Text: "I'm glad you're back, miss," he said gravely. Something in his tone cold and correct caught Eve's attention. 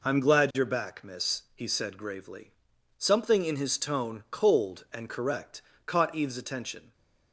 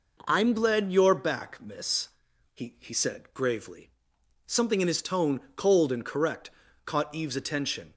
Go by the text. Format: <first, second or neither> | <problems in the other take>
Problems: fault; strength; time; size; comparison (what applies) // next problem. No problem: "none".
first | says "he" twice; at 2.7 s // pauses between "tone" and "cold"; slight; at 5.3 s; 0.16 s long // pauses between "correct" and "caught"; slight; at 6.4 s; 0.36 s long; slight in the first